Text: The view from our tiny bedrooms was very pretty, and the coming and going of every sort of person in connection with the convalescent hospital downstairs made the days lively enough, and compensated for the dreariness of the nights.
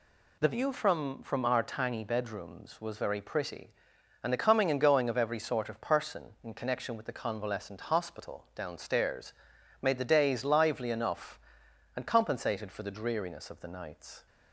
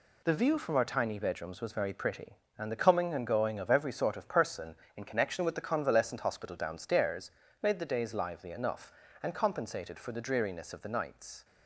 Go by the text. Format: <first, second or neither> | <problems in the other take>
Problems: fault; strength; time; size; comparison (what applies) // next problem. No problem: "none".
second | says "from" twice; at 1.2 s // pauses between "downstairs" and "made"; noticeable; at 9.3 s; 0.50 s long; slight in the second